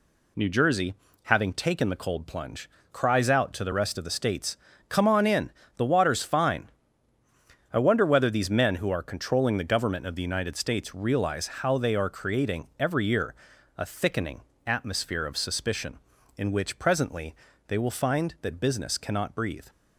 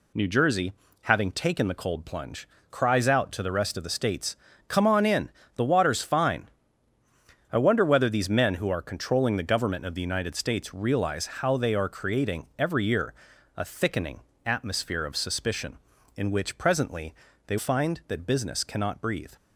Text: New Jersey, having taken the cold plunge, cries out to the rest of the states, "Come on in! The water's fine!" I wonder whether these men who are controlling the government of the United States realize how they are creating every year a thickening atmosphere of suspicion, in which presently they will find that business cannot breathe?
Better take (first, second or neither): first